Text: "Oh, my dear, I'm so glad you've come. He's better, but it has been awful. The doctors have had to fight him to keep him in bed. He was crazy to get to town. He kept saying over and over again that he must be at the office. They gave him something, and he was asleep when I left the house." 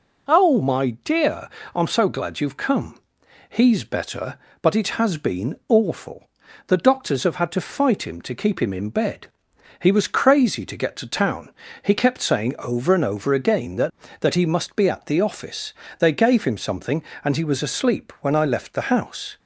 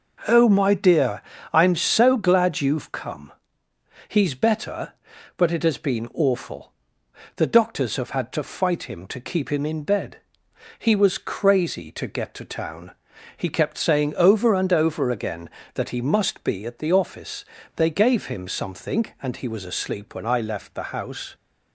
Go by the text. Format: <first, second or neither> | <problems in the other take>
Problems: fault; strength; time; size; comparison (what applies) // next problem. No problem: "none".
second | says "that" twice; at 14.2 s